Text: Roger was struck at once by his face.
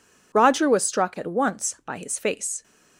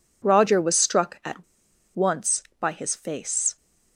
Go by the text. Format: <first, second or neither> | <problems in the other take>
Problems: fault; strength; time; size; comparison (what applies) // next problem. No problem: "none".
first | pauses between "at" and "once"; noticeable; at 1.4 s; 0.49 s long